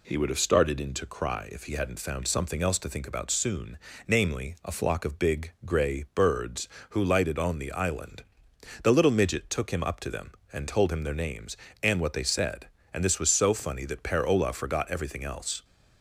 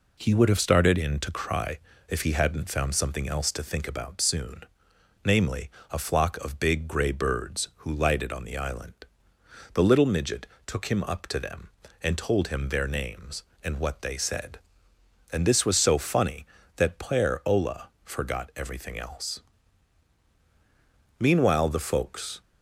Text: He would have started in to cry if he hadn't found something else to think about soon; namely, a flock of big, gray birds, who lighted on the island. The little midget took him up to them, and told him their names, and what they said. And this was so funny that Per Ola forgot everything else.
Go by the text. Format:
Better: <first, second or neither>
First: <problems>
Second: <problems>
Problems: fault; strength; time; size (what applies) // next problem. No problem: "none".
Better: first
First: none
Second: pauses between "cry" and "if"; slight; at 1.7 s; 0.30 s long // pauses between "midget" and "took"; slight; at 10.4 s; 0.20 s long // pauses between "Ola" and "forgot"; slight; at 17.8 s; 0.16 s long // goes on to say "Meanwhile the folks"; noticeable; from 21.2 s on; 1.2 s long